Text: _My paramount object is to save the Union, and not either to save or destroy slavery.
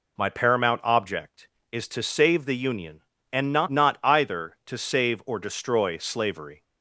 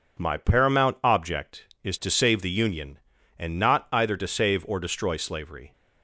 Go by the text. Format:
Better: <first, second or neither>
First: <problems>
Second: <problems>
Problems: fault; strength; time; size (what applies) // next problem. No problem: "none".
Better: second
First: says "not" twice; at 3.7 s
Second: none